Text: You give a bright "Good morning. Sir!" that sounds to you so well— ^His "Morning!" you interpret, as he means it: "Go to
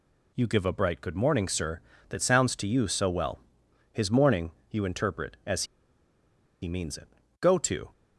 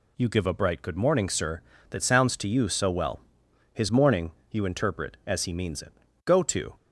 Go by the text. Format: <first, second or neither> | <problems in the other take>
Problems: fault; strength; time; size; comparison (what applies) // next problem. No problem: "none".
second | pauses between "as" and "he"; noticeable; at 5.6 s; 0.96 s long